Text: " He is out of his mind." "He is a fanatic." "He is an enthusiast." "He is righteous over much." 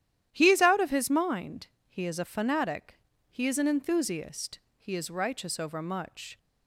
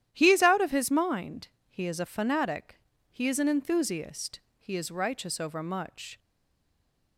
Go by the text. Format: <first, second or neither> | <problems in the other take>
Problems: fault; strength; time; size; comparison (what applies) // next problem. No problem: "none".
first | starts louder than the rest; strong; until 1.1 s; 11.5 dB; strong in the first // stays silent after the last word; from 6.1 s on; 1.0 s long